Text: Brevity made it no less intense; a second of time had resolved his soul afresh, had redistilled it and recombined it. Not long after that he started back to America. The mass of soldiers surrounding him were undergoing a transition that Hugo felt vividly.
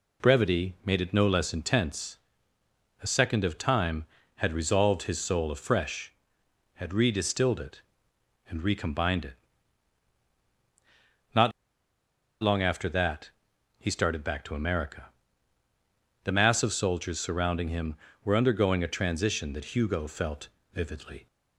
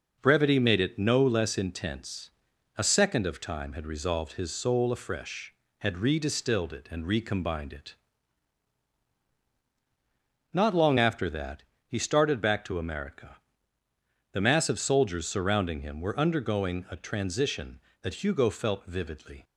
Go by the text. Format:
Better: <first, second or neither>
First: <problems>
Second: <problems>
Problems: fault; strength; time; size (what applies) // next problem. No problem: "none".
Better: second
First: pauses between "Not" and "long"; noticeable; at 11.5 s; 0.91 s long // pauses between "that" and "he"; noticeable; at 13.3 s; 0.46 s long // pauses between "felt" and "vividly"; slight; at 20.4 s; 0.26 s long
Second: pauses between "that" and "he"; slight; at 11.6 s; 0.22 s long